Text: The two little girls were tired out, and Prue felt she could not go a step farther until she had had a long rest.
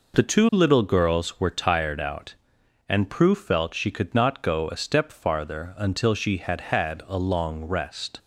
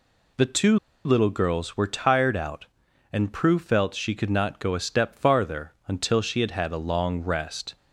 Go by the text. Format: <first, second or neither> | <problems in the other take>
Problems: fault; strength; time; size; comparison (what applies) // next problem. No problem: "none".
first | pauses between "two" and "little"; slight; at 0.7 s; 0.27 s long // pauses between "farther" and "until"; slight; at 5.7 s; 0.16 s long